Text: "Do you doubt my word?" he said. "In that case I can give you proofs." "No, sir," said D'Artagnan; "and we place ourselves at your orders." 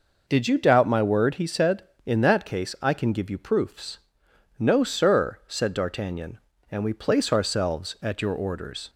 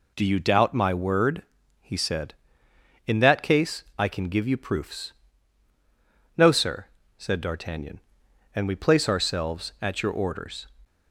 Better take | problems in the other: second | says "Did" for "Do"; at 0.2 s

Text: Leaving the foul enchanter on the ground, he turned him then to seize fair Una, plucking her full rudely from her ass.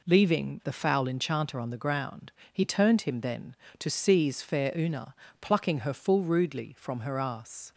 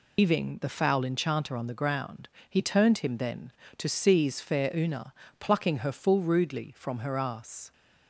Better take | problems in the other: first | loses the start of "Leaving"; at 0.1 s; 145 ms

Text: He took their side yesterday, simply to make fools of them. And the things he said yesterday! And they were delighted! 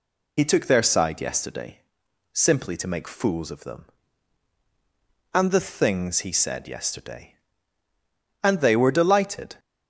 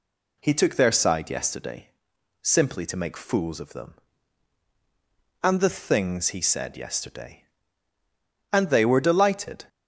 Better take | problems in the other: second | loses the start of "He"; at 0.3 s; 65 ms

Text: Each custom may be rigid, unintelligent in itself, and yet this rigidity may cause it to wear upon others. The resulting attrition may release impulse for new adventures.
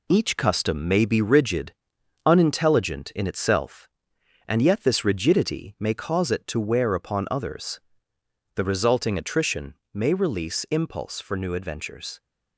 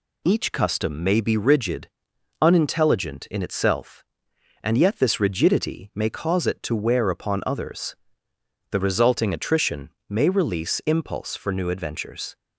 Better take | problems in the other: second | gets quieter; noticeable; throughout; 5.5 dB // pauses between "attrition" and "may"; slight; at 9.7 s; 0.20 s long; slight in the second

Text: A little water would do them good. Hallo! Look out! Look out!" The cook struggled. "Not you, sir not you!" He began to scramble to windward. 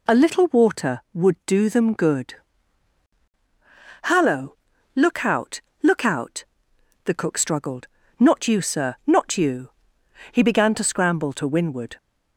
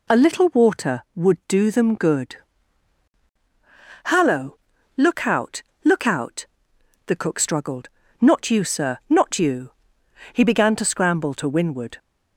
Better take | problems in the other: neither | none

